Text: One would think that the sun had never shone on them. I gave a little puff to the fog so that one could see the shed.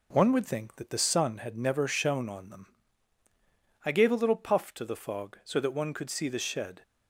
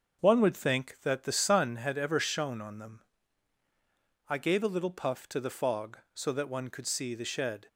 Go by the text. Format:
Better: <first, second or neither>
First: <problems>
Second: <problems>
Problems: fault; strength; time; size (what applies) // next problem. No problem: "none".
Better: first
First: none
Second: starts louder than the rest; noticeable; until 1.2 s; 6 dB // says "ever" for "never"; at 1.9 s